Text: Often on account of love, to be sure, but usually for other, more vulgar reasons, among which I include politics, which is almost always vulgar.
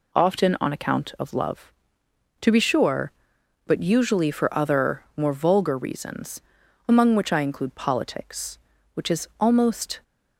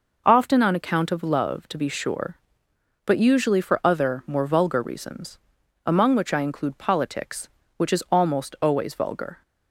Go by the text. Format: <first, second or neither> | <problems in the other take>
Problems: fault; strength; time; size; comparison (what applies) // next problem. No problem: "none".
second | stops before "always vulgar"; at 10.0 s